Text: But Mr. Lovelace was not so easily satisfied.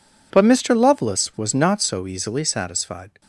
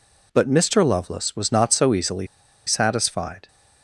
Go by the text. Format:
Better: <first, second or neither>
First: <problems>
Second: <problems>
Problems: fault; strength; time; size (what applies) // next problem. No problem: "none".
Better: first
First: none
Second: pauses between "easily" and "satisfied"; at 2.2 s; 0.40 s long